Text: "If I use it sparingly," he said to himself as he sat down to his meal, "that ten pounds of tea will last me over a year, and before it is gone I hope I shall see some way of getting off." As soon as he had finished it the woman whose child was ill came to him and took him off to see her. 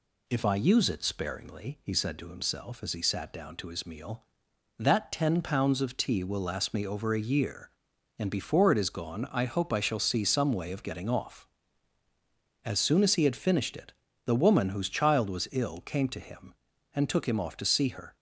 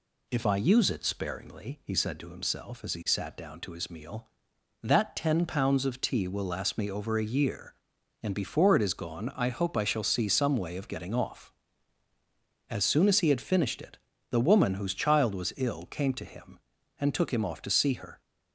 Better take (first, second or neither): neither